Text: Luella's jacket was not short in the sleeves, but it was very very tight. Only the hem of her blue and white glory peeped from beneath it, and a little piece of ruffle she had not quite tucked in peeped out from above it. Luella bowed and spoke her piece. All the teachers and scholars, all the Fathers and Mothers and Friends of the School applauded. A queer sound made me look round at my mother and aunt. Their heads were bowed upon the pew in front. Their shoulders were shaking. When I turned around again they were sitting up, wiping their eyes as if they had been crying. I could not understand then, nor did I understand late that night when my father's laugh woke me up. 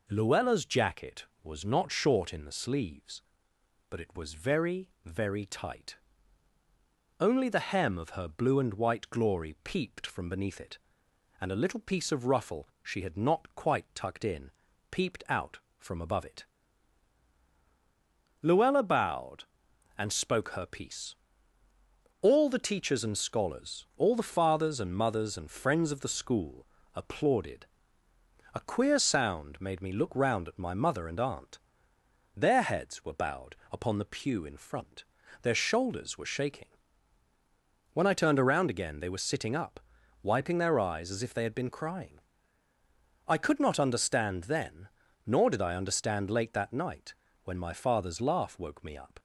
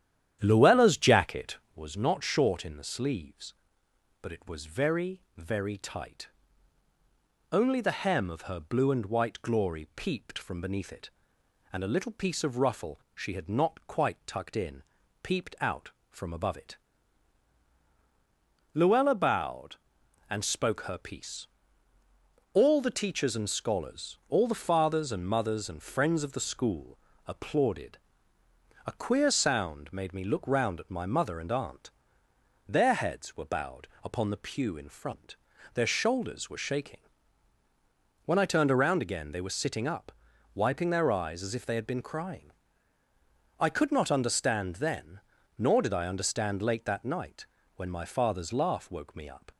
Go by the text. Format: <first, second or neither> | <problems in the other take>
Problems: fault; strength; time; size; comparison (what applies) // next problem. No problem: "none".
first | starts louder than the rest; strong; until 1.8 s; 10.5 dB // pauses between "very" and "very"; slight; at 5.2 s; 0.16 s long; slight in the first // pauses between "in" and "peeped"; at 14.8 s; 0.40 s long; also in the first // pauses between "School" and "applauded"; slight; at 26.9 s; 0.30 s long; slight in the first // pauses between "bowed" and "upon"; slight; at 33.8 s; 0.16 s long; slight in the first // pauses between "night" and "when"; slight; at 47.4 s; 0.32 s long; slight in the first